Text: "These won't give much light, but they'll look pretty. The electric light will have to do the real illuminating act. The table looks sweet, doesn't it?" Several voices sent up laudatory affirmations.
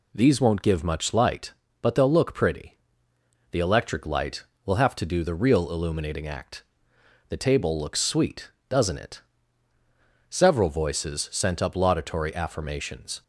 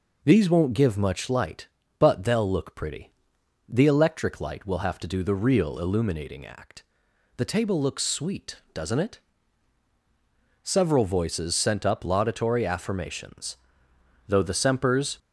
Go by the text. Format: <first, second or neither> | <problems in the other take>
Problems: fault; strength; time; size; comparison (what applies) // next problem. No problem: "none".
first | goes on to say "Though the Sempers"; noticeable; from 14.2 s on; 0.90 s long